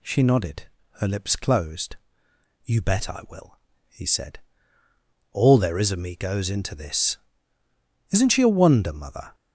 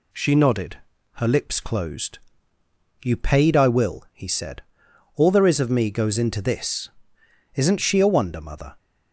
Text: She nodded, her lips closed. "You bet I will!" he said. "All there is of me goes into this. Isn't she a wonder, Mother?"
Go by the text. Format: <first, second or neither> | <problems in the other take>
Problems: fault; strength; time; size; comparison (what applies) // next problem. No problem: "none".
first | says "paid" for "bet"; at 3.1 s